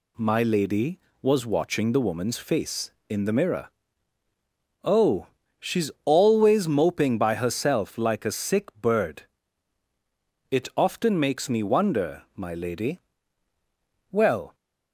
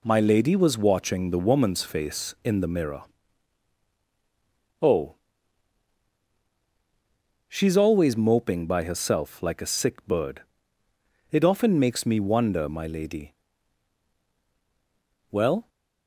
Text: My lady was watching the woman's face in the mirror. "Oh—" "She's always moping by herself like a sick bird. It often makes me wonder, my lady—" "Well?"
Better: neither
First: none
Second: none

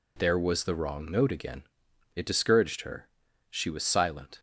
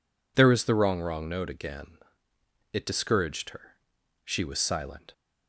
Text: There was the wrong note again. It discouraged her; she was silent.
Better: first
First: none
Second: says "wrong" twice; at 1.0 s

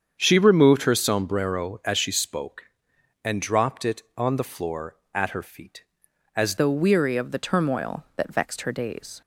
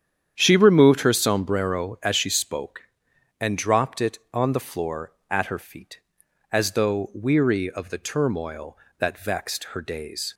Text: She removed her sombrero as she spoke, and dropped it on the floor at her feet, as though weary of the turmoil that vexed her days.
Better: second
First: starts louder than the rest; strong; until 1.2 s; 7.5 dB // changes voice at "though"; from 6.5 s on; 2.7 s long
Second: starts louder than the rest; strong; until 1.3 s; 9 dB

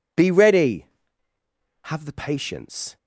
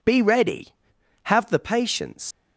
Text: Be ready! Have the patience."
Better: first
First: none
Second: leaves "patience" unfinished; at 2.3 s; 125 ms

